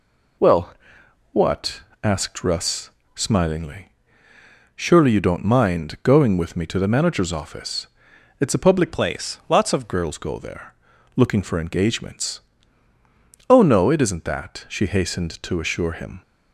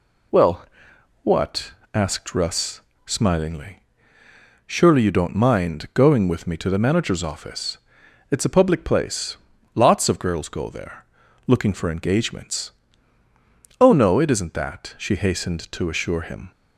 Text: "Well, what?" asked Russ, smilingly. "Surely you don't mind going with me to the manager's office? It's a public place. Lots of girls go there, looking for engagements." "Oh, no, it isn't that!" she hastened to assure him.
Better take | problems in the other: second | changes voice from "place" to "of"; from 8.9 to 9.9 s; 1.0 s long

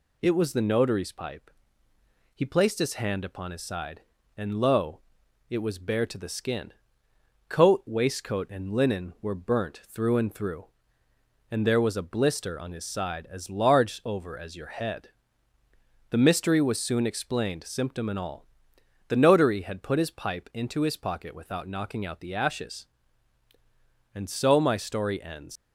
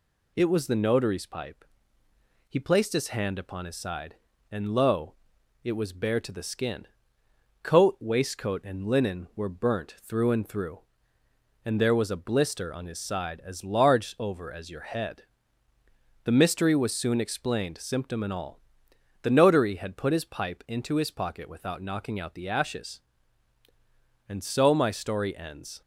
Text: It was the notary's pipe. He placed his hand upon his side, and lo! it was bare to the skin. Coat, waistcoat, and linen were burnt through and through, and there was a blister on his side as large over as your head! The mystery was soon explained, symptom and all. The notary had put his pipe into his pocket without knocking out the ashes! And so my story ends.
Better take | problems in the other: second | leaves "ends" unfinished; at 25.5 s; 115 ms

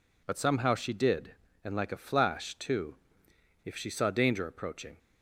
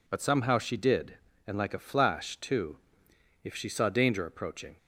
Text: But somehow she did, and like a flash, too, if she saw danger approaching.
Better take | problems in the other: neither | none

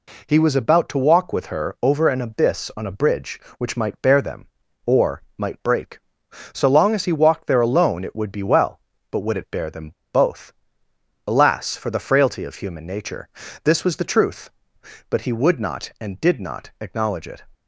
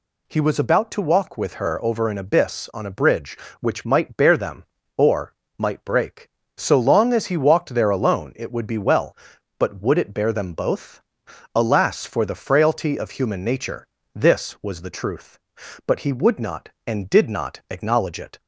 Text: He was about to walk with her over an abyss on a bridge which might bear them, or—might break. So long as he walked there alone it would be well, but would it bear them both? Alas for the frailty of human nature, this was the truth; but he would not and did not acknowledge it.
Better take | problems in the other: second | pauses between "them" and "both"; slight; at 9.9 s; 0.23 s long

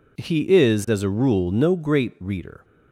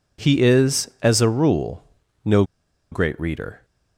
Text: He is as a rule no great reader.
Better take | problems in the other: first | pauses between "rule" and "no"; at 1.8 s; 0.44 s long // pauses between "no" and "great"; noticeable; at 2.4 s; 0.48 s long

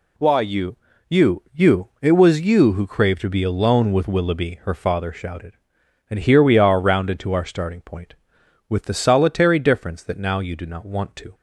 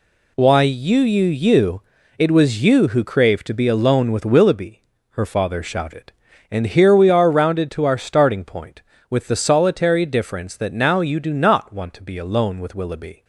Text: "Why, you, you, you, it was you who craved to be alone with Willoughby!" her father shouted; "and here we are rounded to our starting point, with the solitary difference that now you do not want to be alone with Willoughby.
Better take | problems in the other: second | stops before "be alone with Willoughby"; at 11.3 s

